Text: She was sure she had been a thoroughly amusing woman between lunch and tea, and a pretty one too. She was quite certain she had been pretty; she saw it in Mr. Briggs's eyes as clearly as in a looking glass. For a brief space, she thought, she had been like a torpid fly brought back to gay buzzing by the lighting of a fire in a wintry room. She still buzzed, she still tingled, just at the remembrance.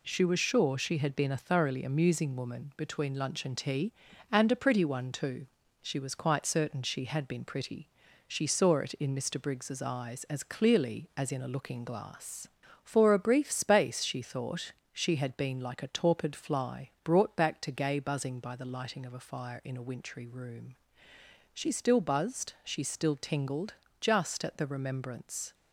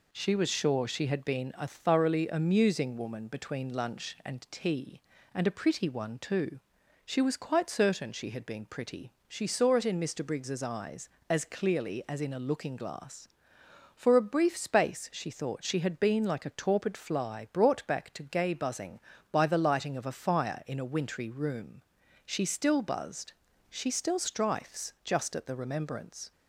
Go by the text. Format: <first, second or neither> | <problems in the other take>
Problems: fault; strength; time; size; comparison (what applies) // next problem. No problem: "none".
first | says "strifes" for "tingled"; at 24.1 s